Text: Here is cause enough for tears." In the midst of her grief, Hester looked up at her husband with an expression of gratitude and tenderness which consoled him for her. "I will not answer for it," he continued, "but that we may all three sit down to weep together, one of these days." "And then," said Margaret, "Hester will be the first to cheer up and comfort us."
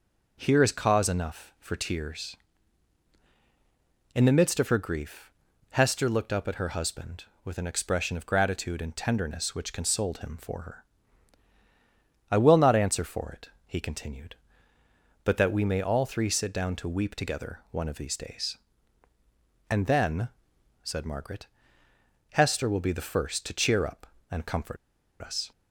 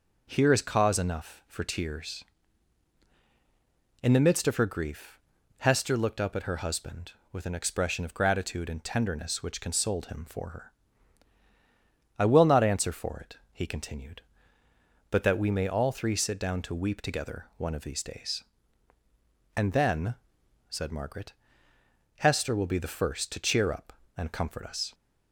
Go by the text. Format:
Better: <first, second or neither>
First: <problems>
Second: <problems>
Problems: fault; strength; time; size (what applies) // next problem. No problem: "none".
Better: second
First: pauses between "comfort" and "us"; at 24.7 s; 0.44 s long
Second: none